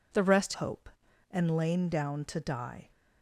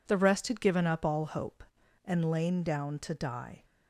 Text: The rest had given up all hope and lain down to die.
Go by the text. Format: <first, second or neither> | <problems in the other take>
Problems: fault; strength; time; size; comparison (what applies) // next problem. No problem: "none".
second | skips "had given up all"; at 0.5 s